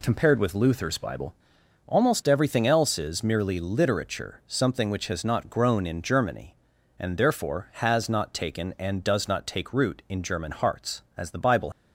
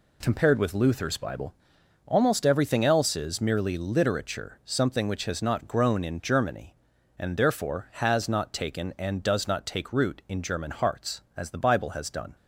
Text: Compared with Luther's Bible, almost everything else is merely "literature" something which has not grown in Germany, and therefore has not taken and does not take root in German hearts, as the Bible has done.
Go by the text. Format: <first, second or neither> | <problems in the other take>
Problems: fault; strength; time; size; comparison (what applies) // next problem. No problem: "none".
second | stops before "has done"; at 11.7 s